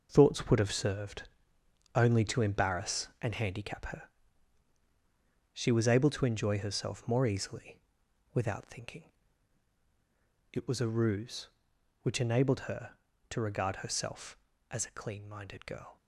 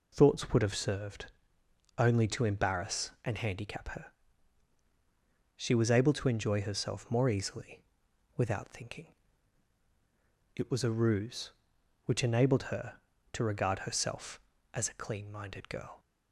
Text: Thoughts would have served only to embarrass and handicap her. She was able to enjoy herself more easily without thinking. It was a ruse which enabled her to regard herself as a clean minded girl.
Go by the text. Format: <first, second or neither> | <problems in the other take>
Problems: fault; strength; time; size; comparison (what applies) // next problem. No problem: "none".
second | gets quieter; strong; throughout; 8.5 dB // pauses between "served" and "only"; noticeable; at 1.2 s; 0.66 s long; noticeable in the second // pauses between "easily" and "without"; noticeable; at 7.7 s; 0.56 s long; noticeable in the second